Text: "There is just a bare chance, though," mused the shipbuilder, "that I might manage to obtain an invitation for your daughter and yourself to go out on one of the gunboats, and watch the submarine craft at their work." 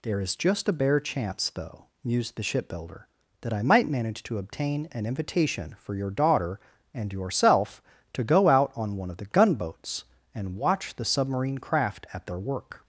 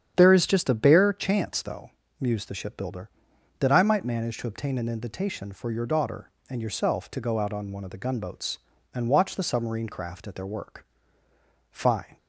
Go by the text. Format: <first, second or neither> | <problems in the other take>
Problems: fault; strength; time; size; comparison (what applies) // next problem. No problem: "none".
first | starts louder than the rest; strong; until 1.1 s; 9 dB // goes on to say "Fine"; slight; from 11.6 s on; 0.48 s long